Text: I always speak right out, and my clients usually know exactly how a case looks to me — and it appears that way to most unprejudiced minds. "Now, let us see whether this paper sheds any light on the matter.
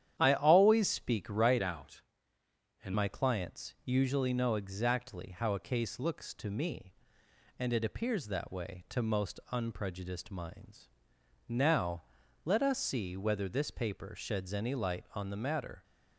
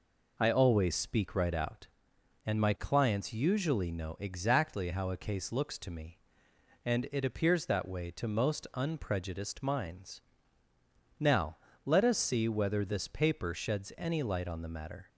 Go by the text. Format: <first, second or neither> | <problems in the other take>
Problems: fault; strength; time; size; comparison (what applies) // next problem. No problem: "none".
second | starts louder than the rest; strong; until 1.2 s; 10.5 dB // changes voice from "out" to "and"; from 1.6 to 2.9 s; 1.3 s long